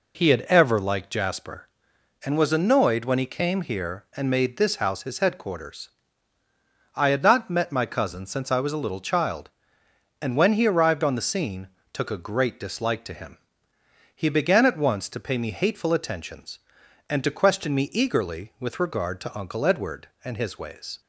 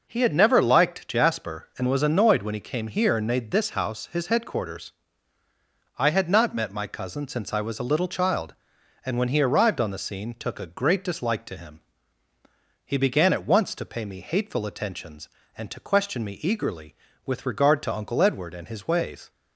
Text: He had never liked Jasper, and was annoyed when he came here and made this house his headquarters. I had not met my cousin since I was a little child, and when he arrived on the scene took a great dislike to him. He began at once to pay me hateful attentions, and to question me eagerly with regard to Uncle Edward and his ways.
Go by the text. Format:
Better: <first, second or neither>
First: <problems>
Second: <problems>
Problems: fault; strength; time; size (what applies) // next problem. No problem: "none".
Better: second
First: says "ever" for "never"; at 0.4 s // pauses between "scene" and "took"; slight; at 11.6 s; 0.24 s long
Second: none